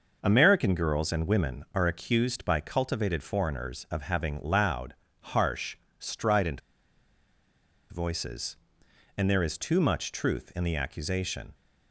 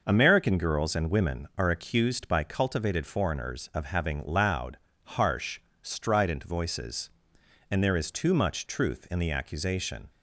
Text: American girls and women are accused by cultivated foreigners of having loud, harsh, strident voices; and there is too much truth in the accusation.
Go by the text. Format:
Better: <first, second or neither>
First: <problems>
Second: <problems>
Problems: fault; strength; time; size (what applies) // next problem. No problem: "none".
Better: second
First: pauses between "strident" and "voices"; strong; at 6.5 s; 1.3 s long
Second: none